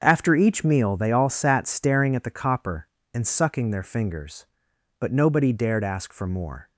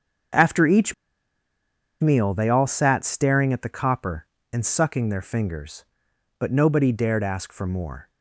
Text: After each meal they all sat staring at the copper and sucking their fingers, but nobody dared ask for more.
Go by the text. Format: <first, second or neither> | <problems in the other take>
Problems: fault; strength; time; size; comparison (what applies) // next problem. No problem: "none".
first | starts louder than the rest; until 2.4 s; 7 dB; also in the first // pauses between "each" and "meal"; at 0.9 s; 1.0 s long